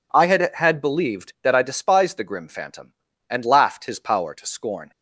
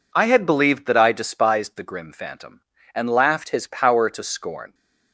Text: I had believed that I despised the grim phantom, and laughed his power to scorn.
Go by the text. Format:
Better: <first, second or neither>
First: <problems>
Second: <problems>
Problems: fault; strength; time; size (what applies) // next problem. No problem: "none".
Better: second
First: says "had" twice; at 0.5 s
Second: none